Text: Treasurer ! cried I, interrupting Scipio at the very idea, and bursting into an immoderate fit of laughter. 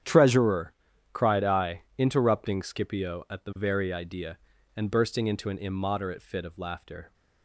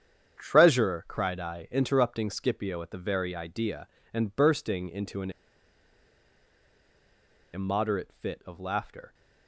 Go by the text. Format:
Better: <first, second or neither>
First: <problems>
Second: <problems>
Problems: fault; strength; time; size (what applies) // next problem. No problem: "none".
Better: first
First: starts louder than the rest; strong; until 1.4 s; 9.5 dB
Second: starts louder than the rest; strong; until 1.4 s; 8.5 dB // pauses between "an" and "immoderate"; strong; at 5.3 s; 2.2 s long